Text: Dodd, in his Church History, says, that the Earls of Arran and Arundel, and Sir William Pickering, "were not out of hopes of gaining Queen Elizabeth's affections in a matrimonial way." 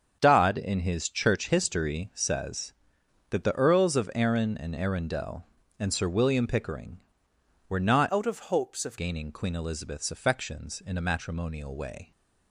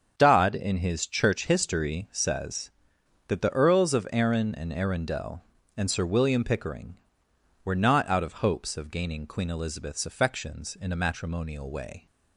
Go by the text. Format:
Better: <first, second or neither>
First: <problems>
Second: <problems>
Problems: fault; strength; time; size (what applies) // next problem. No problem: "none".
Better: second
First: starts louder than the rest; until 1.2 s; 7 dB // changes voice from "out" to "of"; from 8.0 to 8.9 s; 0.9 s long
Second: starts louder than the rest; until 1.1 s; 7 dB